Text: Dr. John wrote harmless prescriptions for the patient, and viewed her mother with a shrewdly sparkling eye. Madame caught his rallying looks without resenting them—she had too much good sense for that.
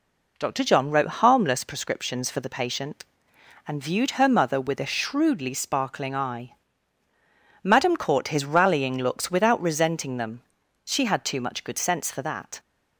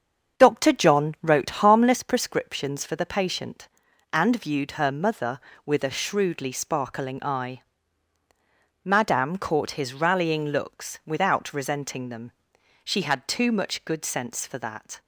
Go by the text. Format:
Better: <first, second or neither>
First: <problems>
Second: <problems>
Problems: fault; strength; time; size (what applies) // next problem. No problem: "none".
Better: first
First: none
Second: starts louder than the rest; until 2.0 s; 7 dB